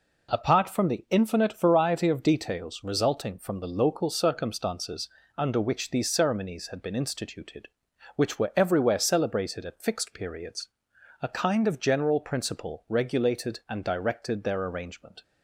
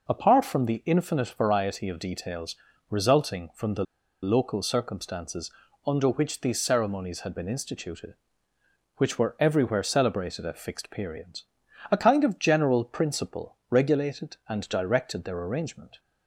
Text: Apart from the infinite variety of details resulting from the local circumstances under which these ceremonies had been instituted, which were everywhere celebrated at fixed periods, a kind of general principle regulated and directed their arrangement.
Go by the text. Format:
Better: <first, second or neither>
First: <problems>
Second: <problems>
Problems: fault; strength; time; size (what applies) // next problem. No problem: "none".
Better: first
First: pauses between "circumstances" and "under"; slight; at 5.0 s; 0.30 s long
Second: pauses between "details" and "resulting"; slight; at 2.5 s; 0.34 s long // pauses between "the" and "local"; at 3.8 s; 0.38 s long // pauses between "circumstances" and "under"; slight; at 5.5 s; 0.34 s long